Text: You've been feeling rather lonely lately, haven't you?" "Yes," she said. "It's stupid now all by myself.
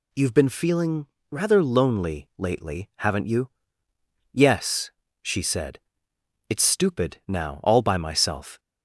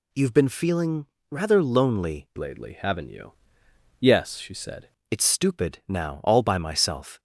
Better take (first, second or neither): first